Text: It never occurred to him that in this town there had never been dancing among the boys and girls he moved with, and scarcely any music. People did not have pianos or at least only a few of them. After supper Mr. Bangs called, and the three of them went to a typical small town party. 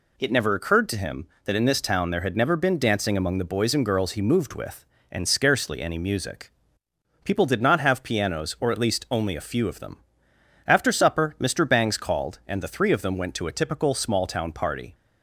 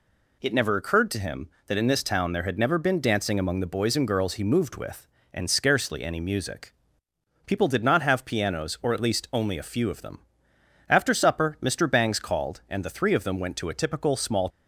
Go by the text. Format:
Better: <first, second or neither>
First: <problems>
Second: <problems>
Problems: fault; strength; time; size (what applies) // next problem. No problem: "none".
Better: first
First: none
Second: stops before "town party"; at 14.5 s